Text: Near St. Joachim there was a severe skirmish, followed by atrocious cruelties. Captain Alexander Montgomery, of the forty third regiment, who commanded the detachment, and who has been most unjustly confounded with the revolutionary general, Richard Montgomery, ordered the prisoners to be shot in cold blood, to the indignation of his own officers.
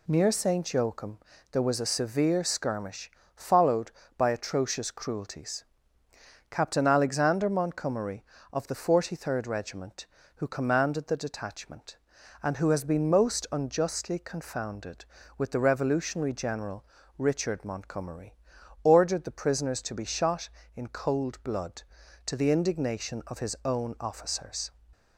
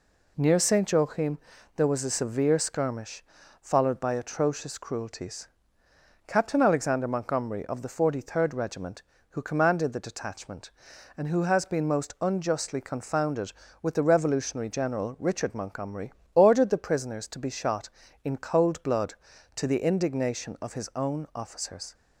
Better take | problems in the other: neither | pauses between "Joachim" and "there"; the same in both

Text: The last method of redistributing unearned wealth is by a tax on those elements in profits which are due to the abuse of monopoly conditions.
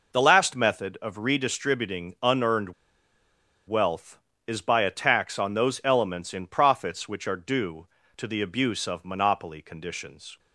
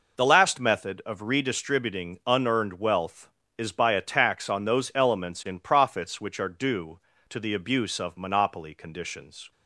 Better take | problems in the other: second | pauses between "unearned" and "wealth"; noticeable; at 2.7 s; 0.94 s long

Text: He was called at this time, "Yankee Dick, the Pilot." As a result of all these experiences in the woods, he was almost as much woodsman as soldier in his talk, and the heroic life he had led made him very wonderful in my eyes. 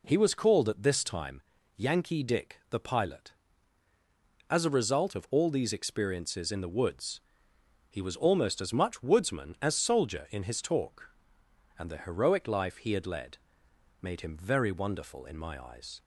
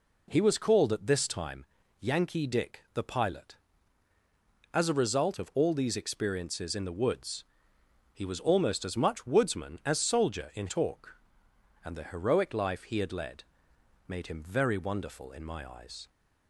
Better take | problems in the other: first | skips "his"; at 10.6 s // pauses between "led" and "made"; noticeable; at 13.4 s; 0.60 s long; noticeable in the first

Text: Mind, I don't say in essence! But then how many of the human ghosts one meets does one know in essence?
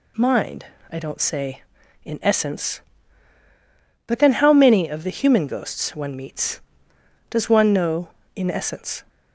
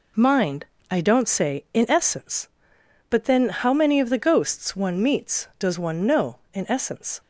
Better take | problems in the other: first | skips "human"; at 4.1 s

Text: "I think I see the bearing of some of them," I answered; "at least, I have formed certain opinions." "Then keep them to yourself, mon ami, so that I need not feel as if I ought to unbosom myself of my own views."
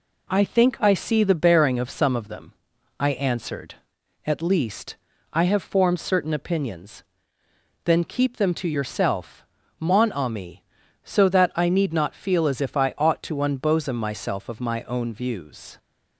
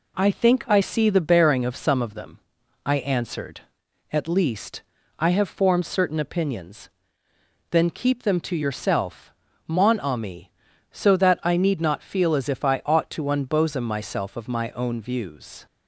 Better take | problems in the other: neither | none

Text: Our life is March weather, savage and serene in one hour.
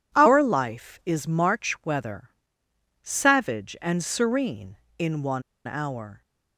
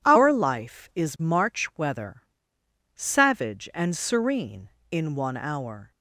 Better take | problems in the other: second | pauses between "one" and "hour"; slight; at 5.4 s; 0.23 s long

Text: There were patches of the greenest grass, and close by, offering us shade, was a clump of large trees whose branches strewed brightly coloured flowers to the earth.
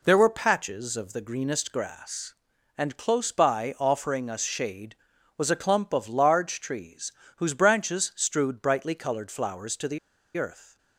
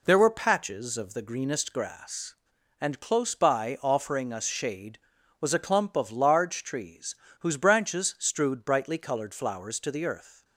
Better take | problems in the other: second | pauses between "trees" and "whose"; slight; at 7.1 s; 0.24 s long; slight in the second // pauses between "the" and "earth"; at 9.9 s; 0.38 s long

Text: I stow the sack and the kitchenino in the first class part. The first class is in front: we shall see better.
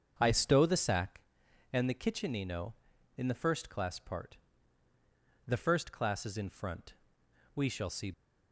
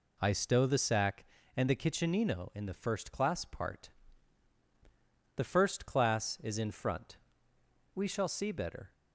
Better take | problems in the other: second | starts louder than the rest; until 1.2 s; 7 dB // stops before "better"; at 8.1 s

